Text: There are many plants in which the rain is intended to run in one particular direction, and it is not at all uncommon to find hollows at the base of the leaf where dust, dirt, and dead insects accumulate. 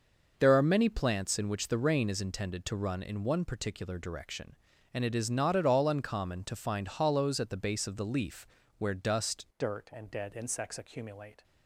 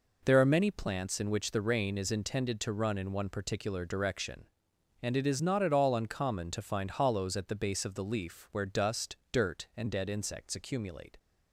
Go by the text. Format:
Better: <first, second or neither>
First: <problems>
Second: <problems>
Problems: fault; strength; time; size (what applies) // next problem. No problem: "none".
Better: second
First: starts louder than the rest; noticeable; until 1.3 s; 6 dB // pauses between "leaf" and "where"; slight; at 8.4 s; 0.32 s long // changes voice at "dirt"; from 9.5 s on; 1.9 s long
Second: none